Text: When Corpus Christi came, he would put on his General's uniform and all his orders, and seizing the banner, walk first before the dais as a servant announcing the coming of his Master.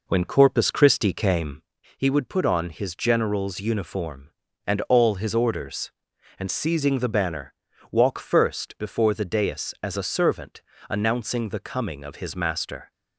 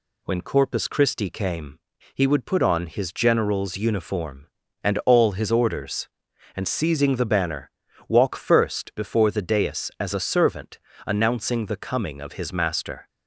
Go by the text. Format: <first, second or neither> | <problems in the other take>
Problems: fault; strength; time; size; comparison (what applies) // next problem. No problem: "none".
second | starts louder than the rest; noticeable; until 1.9 s; 4.5 dB // pauses between "servant" and "announcing"; slight; at 10.6 s; 0.26 s long; slight in the second